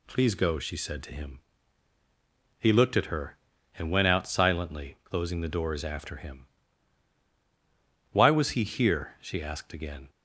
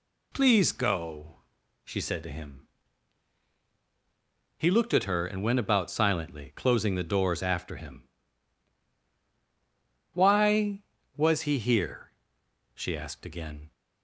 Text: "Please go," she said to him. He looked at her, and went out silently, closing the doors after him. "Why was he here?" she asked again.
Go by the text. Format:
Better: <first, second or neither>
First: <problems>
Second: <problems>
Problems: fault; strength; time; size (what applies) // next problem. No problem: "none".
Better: first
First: none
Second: says "about" for "out"; at 5.5 s